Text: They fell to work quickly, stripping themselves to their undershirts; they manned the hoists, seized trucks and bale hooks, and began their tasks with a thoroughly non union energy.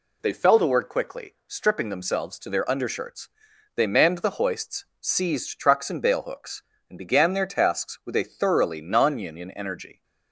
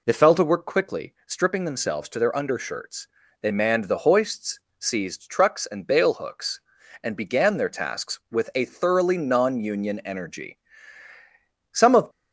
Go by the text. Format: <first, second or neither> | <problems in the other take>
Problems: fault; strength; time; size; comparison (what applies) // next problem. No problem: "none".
first | goes on to say "Some of"; slight; from 11.7 s on; 0.38 s long